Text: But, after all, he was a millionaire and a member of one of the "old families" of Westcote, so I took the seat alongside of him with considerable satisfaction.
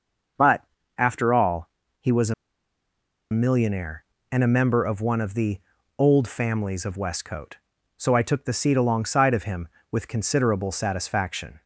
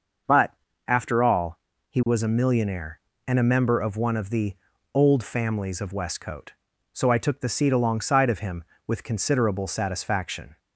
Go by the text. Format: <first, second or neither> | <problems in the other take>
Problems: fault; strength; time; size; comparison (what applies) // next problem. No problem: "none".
second | starts louder than the rest; noticeable; until 2.0 s; 6 dB; noticeable in the second // pauses between "a" and "millionaire"; at 2.3 s; 0.98 s long // pauses between "the" and "old"; at 5.5 s; 0.40 s long; also in the second